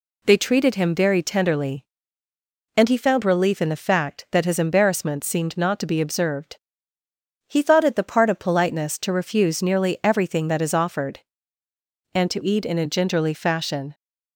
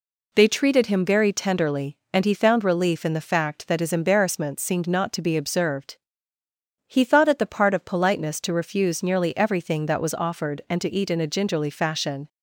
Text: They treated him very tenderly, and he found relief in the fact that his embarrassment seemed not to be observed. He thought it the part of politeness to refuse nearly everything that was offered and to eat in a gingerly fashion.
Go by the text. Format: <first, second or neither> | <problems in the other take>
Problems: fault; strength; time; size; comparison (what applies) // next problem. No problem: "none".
second | says "is" for "was"; at 10.6 s